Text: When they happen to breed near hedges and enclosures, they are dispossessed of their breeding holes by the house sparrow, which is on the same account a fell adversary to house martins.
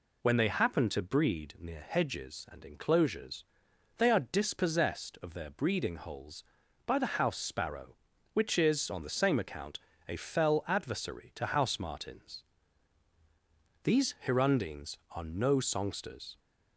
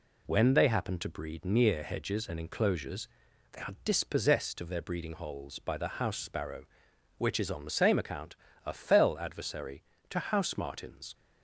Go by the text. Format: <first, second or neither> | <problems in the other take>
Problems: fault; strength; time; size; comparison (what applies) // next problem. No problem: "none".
second | pauses between "account" and "a"; slight; at 9.7 s; 0.30 s long; slight in the second // goes on to say "These hirundines are no songsters"; strong; from 13.8 s on; 2.5 s long